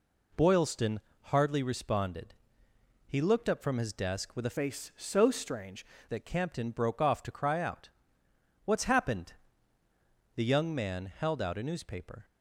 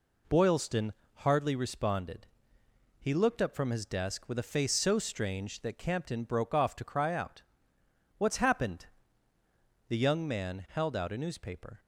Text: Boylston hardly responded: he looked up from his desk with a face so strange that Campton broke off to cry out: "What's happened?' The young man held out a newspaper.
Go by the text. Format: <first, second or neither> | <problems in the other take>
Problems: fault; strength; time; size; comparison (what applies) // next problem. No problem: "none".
second | pauses between "Boylston" and "hardly"; slight; at 0.9 s; 0.26 s long; slight in the second // changes voice from "face" to "strange"; from 4.5 to 5.8 s; 1.3 s long